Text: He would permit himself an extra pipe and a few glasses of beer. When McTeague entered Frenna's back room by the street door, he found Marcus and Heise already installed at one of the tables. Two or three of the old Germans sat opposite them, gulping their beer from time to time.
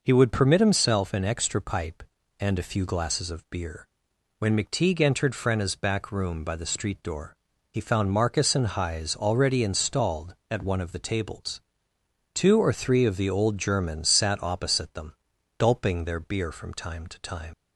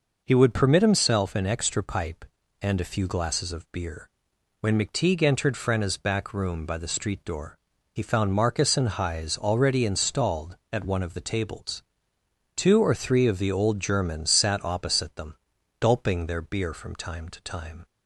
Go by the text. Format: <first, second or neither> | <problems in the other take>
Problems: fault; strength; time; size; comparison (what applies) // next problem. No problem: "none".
second | leaves "time" unfinished; at 17.5 s; 95 ms